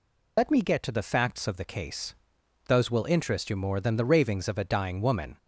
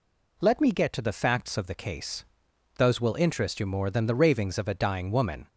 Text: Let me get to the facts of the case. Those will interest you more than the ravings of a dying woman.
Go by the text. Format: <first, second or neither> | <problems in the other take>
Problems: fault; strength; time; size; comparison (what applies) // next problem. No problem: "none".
second | loses the start of "Let"; at 0.3 s; 80 ms